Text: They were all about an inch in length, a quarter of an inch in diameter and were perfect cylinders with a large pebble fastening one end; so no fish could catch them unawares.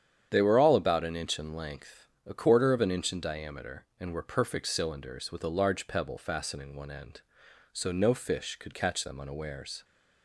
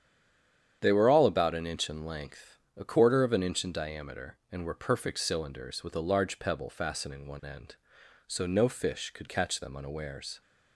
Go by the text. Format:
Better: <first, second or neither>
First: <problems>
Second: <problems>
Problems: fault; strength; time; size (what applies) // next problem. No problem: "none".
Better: first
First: starts louder than the rest; strong; until 1.3 s; 9 dB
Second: stays silent before the first word; slight; until 0.8 s; 0.8 s long // starts louder than the rest; strong; until 1.8 s; 9 dB